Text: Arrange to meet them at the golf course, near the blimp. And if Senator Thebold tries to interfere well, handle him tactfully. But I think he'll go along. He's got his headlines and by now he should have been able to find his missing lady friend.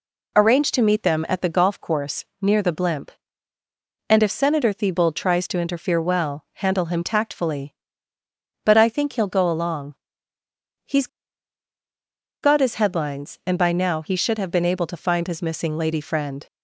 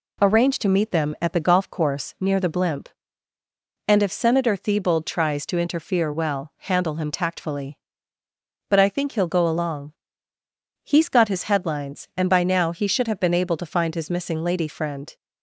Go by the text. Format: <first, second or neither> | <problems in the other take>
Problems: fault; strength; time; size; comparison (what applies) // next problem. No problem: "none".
second | pauses between "He's" and "got"; strong; at 11.0 s; 1.3 s long